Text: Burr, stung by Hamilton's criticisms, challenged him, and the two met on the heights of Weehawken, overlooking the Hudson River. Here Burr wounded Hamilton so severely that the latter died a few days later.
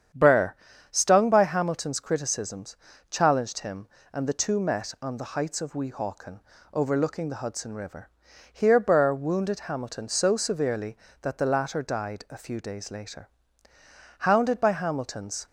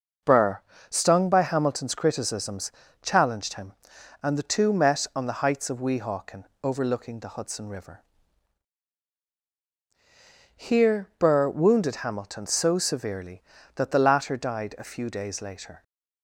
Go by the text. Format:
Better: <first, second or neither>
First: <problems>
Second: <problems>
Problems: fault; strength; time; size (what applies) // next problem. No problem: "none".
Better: second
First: starts louder than the rest; strong; until 1.4 s; 8.5 dB // goes on to say "Hounded by Hamilton's"; noticeable; from 14.1 s on; 1.2 s long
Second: none